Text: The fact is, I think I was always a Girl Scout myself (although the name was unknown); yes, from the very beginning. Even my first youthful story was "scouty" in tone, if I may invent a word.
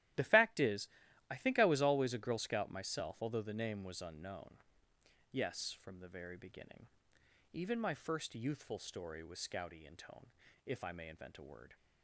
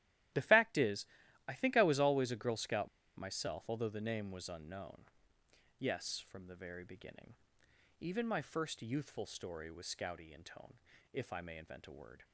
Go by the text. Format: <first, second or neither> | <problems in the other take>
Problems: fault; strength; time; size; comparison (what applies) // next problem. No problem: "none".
first | starts louder than the rest; strong; until 1.7 s; 13.5 dB; strong in the first // pauses between "Scout" and "myself"; slight; at 2.8 s; 0.28 s long